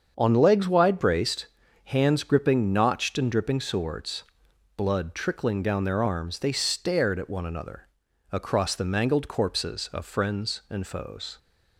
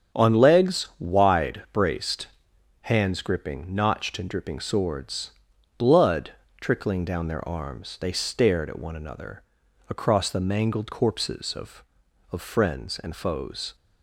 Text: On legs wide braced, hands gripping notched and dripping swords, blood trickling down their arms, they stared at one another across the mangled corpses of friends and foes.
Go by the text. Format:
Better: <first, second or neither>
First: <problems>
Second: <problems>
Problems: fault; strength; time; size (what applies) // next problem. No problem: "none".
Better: first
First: starts louder than the rest; strong; until 1.1 s; 7 dB // pauses between "another" and "across"; at 7.8 s; 0.44 s long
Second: starts louder than the rest; strong; until 1.2 s; 7.5 dB // pauses between "blood" and "trickling"; slight; at 6.3 s; 0.28 s long // pauses between "another" and "across"; at 9.4 s; 0.44 s long // says "of" twice; at 12.3 s